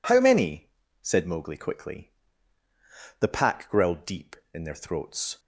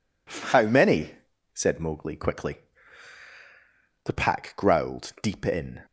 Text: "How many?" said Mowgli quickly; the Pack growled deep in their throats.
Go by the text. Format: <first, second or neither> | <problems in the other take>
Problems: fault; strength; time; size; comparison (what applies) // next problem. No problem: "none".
first | stops before "their throats"; at 5.8 s